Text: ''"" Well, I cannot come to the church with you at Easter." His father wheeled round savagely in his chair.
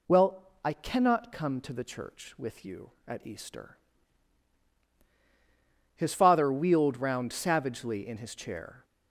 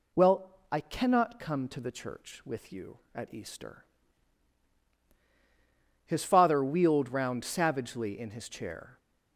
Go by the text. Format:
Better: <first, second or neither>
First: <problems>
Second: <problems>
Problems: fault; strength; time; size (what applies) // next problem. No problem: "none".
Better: neither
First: none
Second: none